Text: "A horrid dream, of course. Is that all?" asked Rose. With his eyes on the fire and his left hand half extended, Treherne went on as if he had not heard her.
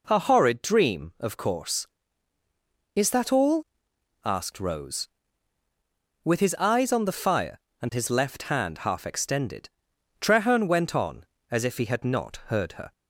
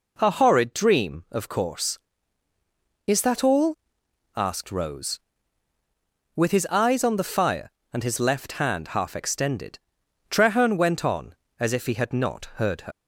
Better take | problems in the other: first | leaves "her" unfinished; at 12.9 s; 85 ms

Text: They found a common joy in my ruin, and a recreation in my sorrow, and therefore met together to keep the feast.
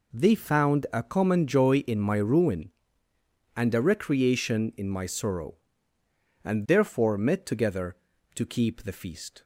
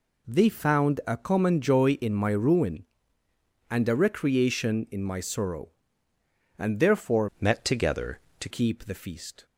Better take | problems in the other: first | changes voice from "met" to "to"; from 7.3 to 8.4 s; 1.1 s long

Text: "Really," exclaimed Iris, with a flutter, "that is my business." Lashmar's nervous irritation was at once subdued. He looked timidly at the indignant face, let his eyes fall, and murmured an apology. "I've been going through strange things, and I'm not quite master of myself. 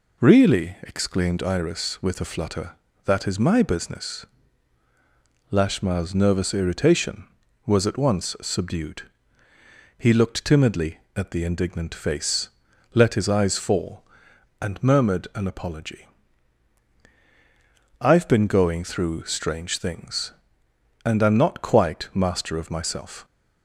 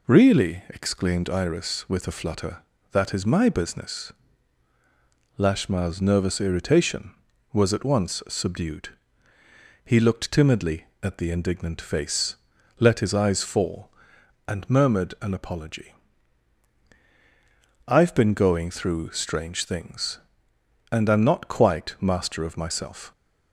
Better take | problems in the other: neither | none

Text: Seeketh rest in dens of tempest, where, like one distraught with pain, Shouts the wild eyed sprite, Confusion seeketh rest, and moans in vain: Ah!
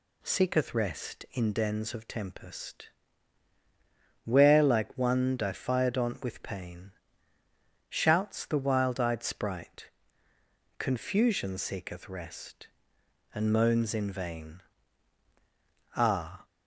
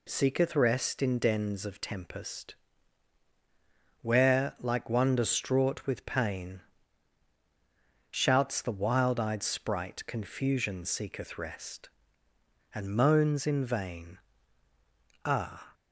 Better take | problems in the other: second | says "diphyodont" for "distraught"; at 5.3 s

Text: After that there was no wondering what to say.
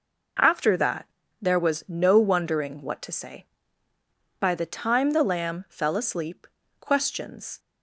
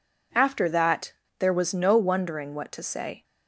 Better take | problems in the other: second | pauses between "that" and "there"; slight; at 1.0 s; 0.34 s long; slight in the second // goes on to say "By the time the lamb fell asleep questions"; strong; from 4.3 s on; 3.2 s long

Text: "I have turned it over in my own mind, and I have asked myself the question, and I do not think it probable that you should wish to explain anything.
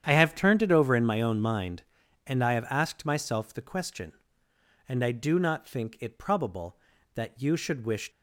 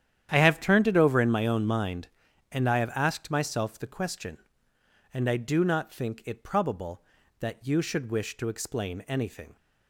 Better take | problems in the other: second | starts louder than the rest; strong; until 1.0 s; 9.5 dB; strong in the second // stops before "to explain anything"; at 8.1 s

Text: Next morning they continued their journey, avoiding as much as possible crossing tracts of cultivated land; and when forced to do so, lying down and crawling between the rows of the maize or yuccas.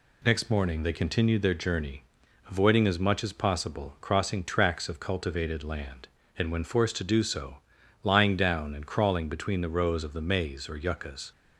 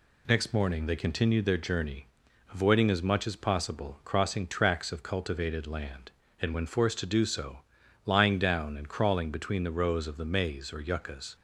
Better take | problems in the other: neither | none

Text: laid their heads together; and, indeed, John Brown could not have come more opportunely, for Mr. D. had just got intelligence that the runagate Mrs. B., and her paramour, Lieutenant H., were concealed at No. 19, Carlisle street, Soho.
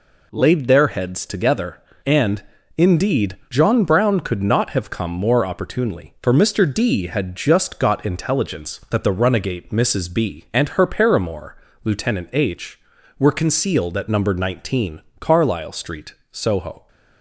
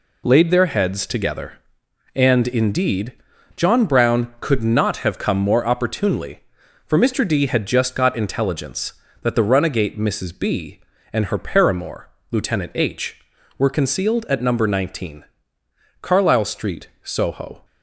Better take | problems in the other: neither | none

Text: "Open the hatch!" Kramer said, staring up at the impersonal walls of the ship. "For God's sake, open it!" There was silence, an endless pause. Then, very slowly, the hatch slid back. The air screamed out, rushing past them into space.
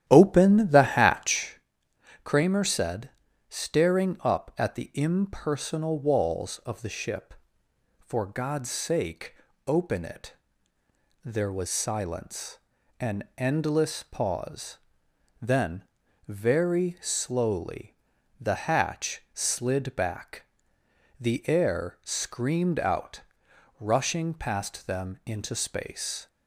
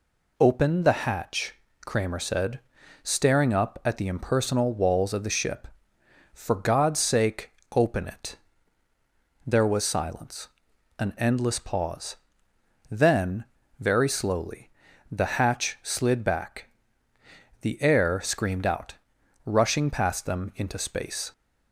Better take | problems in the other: second | starts louder than the rest; strong; until 1.5 s; 11.5 dB

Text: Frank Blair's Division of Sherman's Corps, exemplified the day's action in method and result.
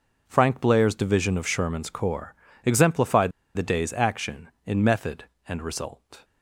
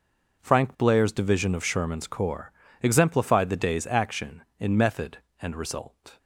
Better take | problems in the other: second | pauses between "exemplified" and "the"; slight; at 3.3 s; 0.24 s long

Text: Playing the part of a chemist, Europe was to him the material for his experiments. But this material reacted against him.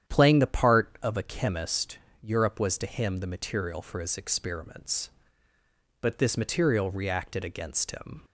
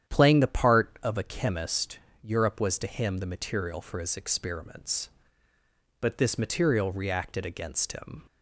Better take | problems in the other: neither | starts louder than the rest; strong; the same in both

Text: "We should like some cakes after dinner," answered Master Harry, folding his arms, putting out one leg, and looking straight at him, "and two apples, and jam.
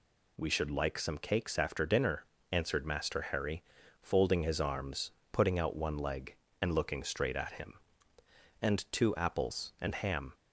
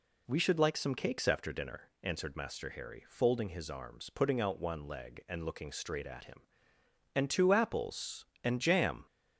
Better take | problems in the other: second | says "ham" for "jam"; at 9.9 s

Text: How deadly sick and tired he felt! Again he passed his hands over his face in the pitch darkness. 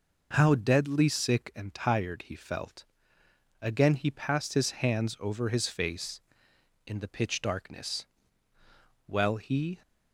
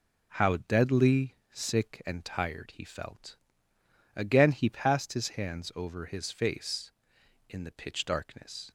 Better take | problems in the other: second | goes on to say "Well he"; noticeable; from 9.0 s on; 0.76 s long

